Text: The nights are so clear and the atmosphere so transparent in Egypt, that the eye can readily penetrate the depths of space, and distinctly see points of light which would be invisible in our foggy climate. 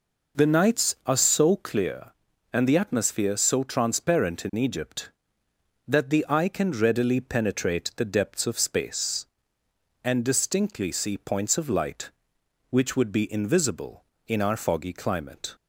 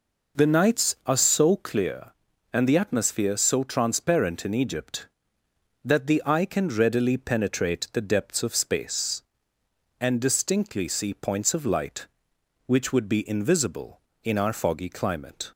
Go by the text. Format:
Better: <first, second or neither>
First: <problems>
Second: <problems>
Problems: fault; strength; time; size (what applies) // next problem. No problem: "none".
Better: neither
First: none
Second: none